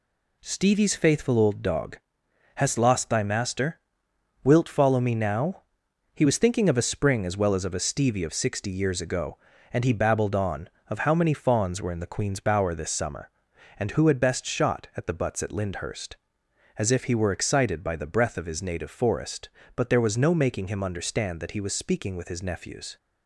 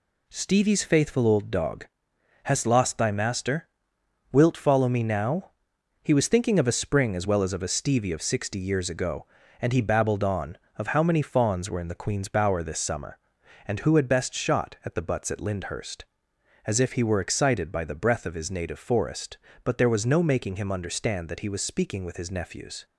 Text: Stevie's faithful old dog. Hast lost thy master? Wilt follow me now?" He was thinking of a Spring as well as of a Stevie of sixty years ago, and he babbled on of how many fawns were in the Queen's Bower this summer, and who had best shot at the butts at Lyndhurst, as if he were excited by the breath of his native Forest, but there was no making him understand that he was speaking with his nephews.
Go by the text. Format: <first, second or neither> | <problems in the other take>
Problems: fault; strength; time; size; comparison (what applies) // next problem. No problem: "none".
neither | none